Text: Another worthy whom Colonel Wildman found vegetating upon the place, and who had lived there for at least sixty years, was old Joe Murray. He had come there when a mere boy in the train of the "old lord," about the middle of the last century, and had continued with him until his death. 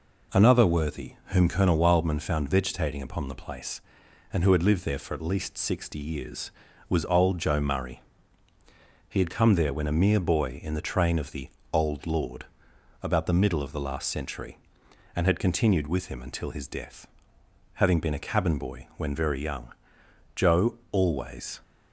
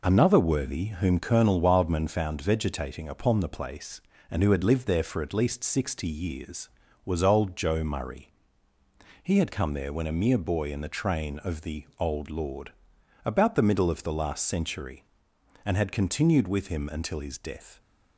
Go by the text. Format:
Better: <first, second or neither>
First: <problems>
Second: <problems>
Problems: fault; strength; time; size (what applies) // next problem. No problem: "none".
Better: second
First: pauses between "the" and "old"; slight; at 11.4 s; 0.24 s long // goes on to say "Having been a cabin boy when very young Joe always"; strong; from 17.7 s on; 3.8 s long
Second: none